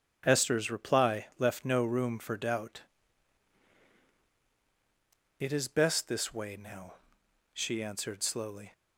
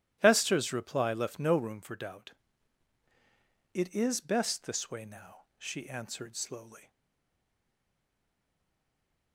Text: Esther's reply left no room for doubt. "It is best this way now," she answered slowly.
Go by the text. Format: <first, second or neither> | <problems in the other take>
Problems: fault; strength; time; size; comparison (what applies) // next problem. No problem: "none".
first | starts louder than the rest; strong; until 1.2 s; 13.5 dB; strong in the first // stays silent after the last word; from 6.9 s on; 2.4 s long